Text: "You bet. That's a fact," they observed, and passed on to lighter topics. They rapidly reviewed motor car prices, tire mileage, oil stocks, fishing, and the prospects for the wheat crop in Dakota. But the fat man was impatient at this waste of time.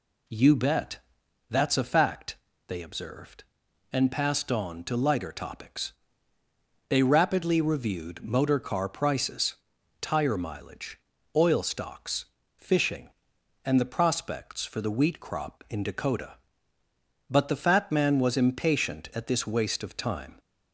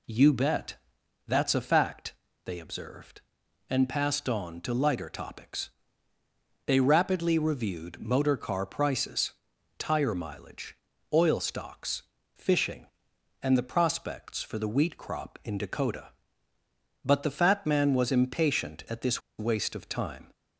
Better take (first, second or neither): first